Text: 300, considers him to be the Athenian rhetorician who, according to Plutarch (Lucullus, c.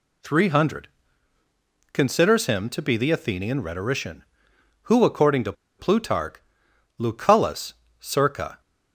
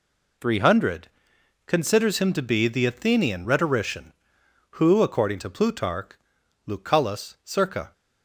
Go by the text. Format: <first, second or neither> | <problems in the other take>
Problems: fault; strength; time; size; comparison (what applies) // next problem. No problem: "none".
second | pauses between "to" and "Plutarch"; slight; at 5.5 s; 0.26 s long